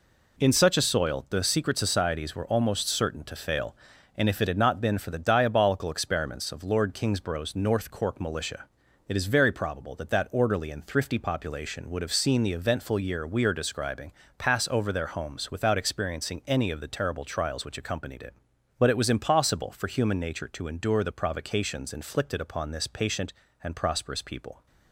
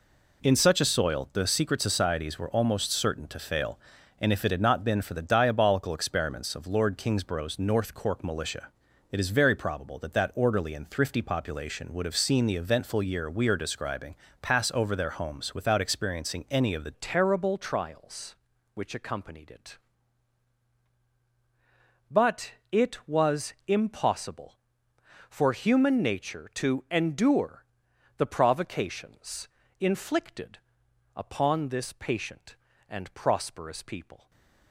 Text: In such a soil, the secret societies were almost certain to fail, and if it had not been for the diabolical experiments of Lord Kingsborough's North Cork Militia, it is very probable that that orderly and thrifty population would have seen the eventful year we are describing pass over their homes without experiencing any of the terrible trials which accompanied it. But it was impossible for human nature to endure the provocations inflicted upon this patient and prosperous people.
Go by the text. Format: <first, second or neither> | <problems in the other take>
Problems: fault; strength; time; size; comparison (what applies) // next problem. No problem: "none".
first | pauses between "describing" and "pass"; slight; at 14.1 s; 0.26 s long; slight in the first // changes voice at "terrible"; from 16.9 s on; 17.3 s long // pauses between "But" and "it"; slight; at 22.5 s; 0.20 s long // pauses between "was" and "impossible"; slight; at 23.5 s; 0.16 s long // pauses between "endure" and "the"; noticeable; at 27.6 s; 0.50 s long // pauses between "provocations" and "inflicted"; slight; at 29.4 s; 0.30 s long // pauses between "inflicted" and "upon"; noticeable; at 30.5 s; 0.56 s long // stays silent after the last word; slight; from 34.1 s on; 0.6 s long